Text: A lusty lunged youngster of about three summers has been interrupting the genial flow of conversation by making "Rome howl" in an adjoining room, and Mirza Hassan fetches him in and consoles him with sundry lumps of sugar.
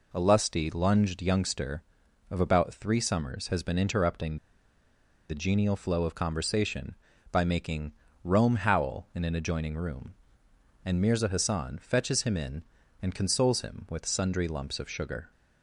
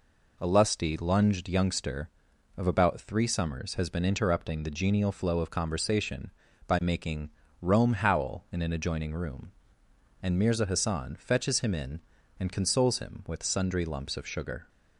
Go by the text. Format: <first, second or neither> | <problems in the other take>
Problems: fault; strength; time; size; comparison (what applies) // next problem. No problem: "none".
second | pauses between "interrupting" and "the"; noticeable; at 4.3 s; 0.92 s long // pauses between "making" and "Rome"; slight; at 7.9 s; 0.32 s long; slight in the second